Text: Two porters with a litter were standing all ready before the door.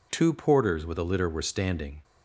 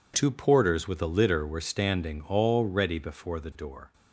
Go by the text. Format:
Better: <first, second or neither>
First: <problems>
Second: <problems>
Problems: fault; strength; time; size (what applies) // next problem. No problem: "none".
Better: second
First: stops before "all ready before the door"; at 2.0 s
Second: none